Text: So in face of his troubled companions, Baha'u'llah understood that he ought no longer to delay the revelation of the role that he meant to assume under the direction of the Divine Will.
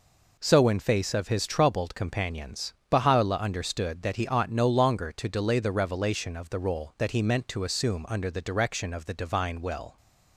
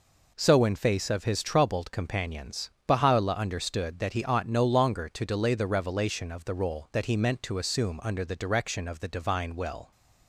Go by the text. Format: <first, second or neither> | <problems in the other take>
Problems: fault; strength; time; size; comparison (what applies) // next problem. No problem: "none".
neither | none